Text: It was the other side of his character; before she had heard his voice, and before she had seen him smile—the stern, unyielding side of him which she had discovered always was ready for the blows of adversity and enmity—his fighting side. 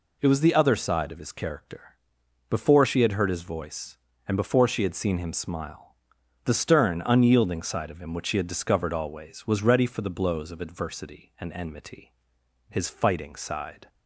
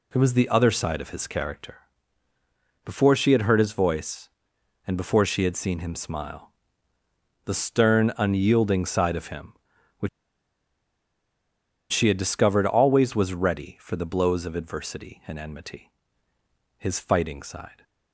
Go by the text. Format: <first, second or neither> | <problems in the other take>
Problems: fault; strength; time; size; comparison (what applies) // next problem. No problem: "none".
first | pauses between "which" and "she"; strong; at 10.0 s; 1.8 s long